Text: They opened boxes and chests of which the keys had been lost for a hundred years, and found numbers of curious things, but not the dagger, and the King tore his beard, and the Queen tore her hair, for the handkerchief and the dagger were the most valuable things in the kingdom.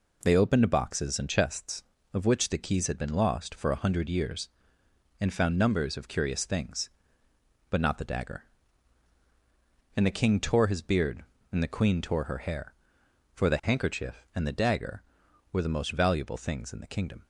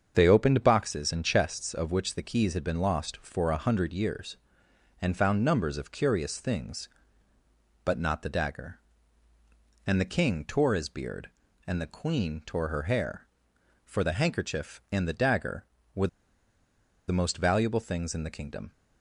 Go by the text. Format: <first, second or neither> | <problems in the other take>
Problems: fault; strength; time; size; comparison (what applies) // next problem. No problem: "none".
first | starts louder than the rest; until 1.1 s; 7 dB // pauses between "were" and "the"; at 16.0 s; 1.0 s long